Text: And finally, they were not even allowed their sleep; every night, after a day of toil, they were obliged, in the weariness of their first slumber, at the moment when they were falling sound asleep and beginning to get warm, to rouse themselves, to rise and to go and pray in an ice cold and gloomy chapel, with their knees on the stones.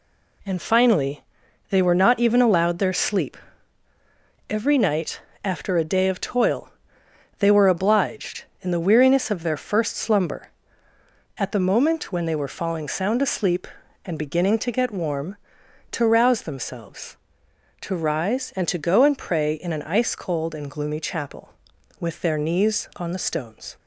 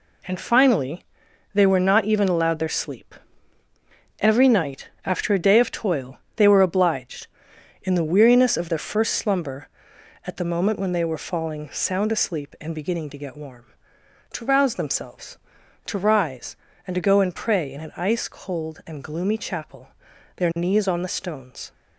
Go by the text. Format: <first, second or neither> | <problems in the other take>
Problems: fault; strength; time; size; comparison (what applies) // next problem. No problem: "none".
first | skips "with"; at 20.1 s